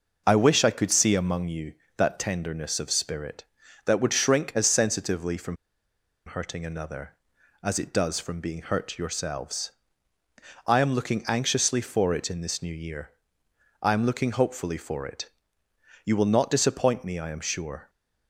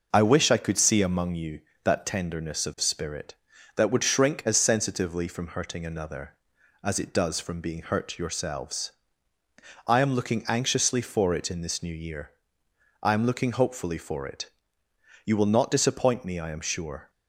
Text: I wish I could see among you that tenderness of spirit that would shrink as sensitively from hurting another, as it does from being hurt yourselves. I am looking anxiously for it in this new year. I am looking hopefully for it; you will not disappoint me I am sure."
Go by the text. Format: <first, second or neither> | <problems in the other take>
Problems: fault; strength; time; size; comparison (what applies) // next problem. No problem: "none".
second | pauses between "from" and "hurting"; noticeable; at 5.5 s; 0.71 s long